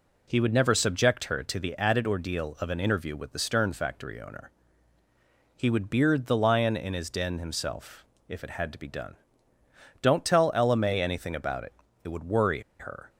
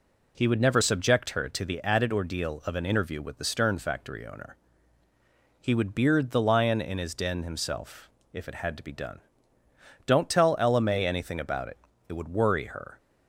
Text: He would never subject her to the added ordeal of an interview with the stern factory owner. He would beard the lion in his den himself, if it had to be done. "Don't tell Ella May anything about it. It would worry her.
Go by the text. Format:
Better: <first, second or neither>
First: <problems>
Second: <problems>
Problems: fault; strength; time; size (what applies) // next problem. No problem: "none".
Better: second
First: pauses between "worry" and "her"; slight; at 12.6 s; 0.18 s long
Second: none